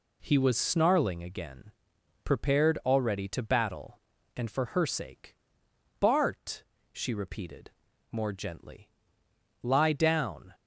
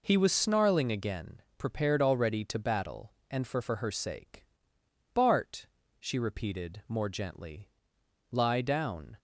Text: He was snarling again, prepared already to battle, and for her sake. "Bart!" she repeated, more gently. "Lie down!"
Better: first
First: none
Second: says "for" twice; at 3.6 s

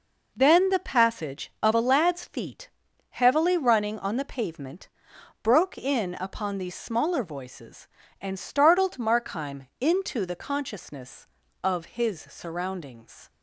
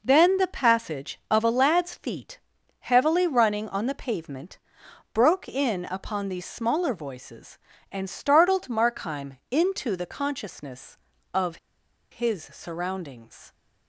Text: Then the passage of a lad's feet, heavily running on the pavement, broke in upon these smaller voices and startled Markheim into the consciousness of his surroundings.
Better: first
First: none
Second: pauses between "of" and "his"; noticeable; at 11.5 s; 0.55 s long

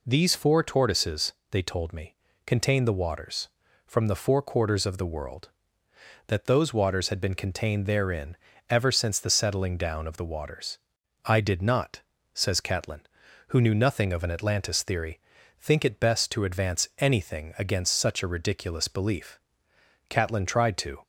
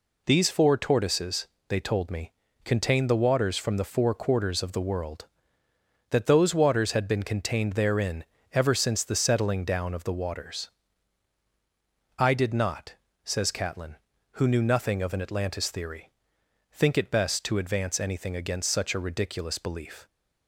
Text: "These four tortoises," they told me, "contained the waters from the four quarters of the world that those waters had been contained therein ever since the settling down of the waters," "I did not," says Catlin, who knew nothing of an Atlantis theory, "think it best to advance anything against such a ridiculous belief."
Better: second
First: pauses between "therein" and "ever"; slight; at 8.3 s; 0.36 s long // goes on to say "Catlin tried to"; noticeable; from 20.0 s on; 0.94 s long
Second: pauses between "therein" and "ever"; slight; at 8.2 s; 0.28 s long

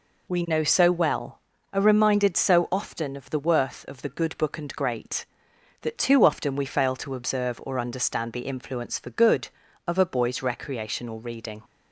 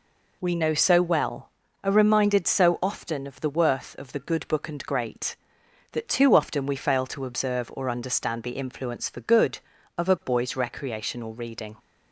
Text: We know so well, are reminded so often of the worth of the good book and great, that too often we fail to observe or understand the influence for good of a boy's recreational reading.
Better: neither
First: none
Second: none

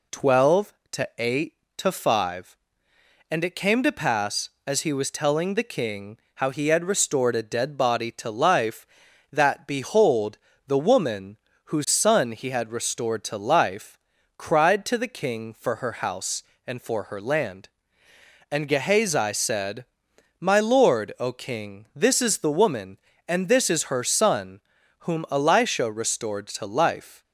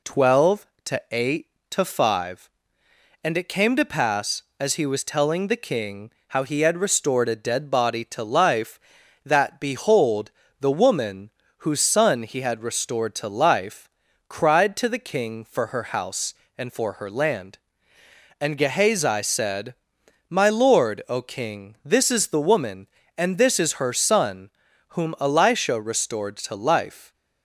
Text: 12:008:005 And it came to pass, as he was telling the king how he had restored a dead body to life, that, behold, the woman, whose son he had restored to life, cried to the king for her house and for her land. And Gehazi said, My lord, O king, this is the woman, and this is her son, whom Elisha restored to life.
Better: neither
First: pauses between "king" and "how"; slight; at 6.1 s; 0.18 s long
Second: pauses between "king" and "how"; slight; at 6.1 s; 0.18 s long

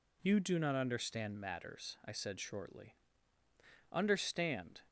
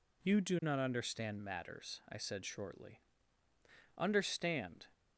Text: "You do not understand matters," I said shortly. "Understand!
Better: neither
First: none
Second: none

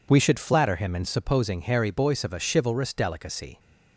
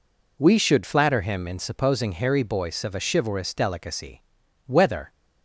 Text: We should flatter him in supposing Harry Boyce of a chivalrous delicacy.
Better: first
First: none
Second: goes on to say "Whether"; slight; from 4.6 s on; 0.42 s long

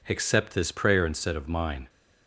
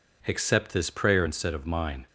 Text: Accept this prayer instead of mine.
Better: neither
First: none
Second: none

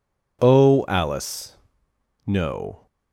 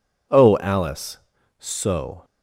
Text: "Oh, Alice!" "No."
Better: first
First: none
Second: says "So" for "No"; at 1.5 s

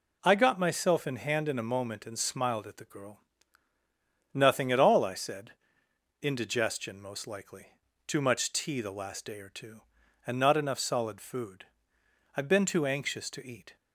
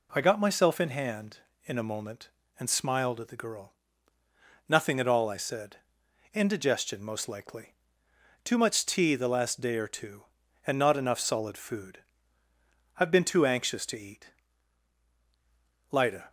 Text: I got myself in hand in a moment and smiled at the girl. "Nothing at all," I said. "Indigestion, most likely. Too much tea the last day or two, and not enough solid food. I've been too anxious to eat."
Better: first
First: none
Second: goes on to say "Lida"; slight; from 15.9 s on; 0.38 s long

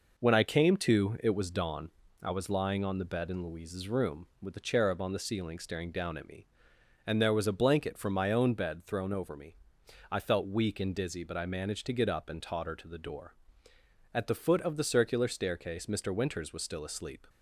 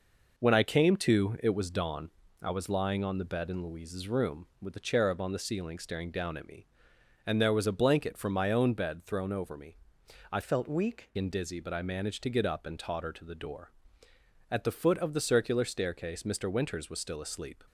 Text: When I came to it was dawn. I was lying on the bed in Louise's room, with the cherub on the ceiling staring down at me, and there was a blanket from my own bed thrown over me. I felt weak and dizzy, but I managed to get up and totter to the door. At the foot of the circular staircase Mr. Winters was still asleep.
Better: first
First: none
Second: changes voice from "felt" to "weak"; from 10.4 to 11.0 s; 0.6 s long

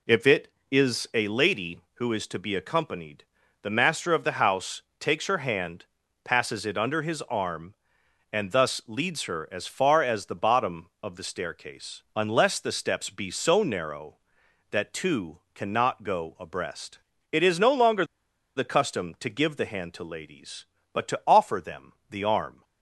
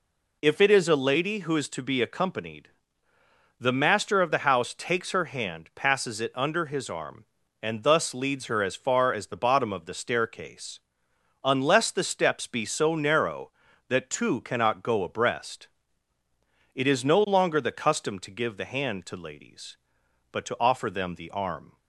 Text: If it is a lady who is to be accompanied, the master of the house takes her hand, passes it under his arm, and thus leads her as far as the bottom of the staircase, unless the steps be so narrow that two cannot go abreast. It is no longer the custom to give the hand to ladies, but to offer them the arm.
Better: second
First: pauses between "house" and "takes"; slight; at 4.8 s; 0.18 s long // pauses between "two" and "cannot"; slight; at 15.3 s; 0.16 s long // pauses between "longer" and "the"; noticeable; at 18.0 s; 0.53 s long // pauses between "them" and "the"; slight; at 21.9 s; 0.16 s long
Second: none

